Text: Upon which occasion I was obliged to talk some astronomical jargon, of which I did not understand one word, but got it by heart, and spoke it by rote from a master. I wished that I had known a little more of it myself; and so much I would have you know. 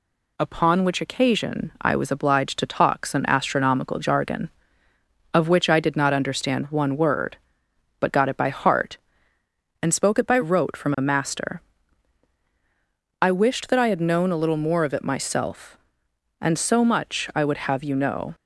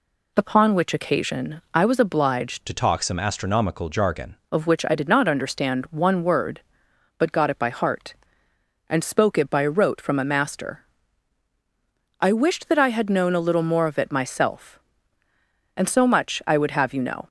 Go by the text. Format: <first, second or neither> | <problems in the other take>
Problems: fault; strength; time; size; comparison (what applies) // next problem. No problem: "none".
first | changes voice from "to" to "jargon"; from 2.6 to 4.3 s; 1.7 s long